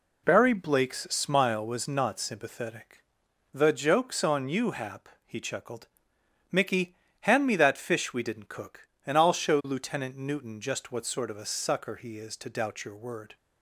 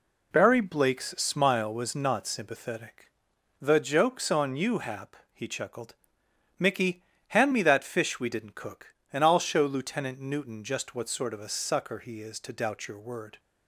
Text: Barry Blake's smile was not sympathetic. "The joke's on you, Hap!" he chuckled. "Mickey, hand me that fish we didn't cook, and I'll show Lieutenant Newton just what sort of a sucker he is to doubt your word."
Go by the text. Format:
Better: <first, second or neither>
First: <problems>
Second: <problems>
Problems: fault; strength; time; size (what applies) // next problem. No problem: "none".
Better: neither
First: none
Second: none